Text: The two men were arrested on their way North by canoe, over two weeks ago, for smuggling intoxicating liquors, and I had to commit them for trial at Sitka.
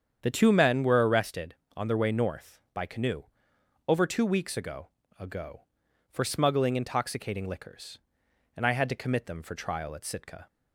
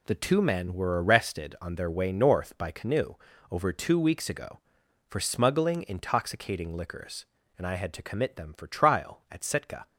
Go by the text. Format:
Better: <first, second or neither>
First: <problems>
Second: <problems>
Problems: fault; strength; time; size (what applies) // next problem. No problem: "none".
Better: second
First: starts louder than the rest; strong; until 1.2 s; 8 dB // says "ago" twice; at 5.1 s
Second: none